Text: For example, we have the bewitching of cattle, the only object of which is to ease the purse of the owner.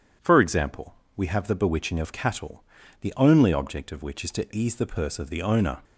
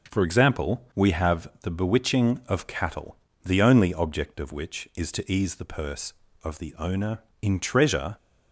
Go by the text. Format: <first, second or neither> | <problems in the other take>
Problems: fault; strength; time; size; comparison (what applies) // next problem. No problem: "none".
first | goes on to say "In treasure"; noticeable; from 7.4 s on; 0.74 s long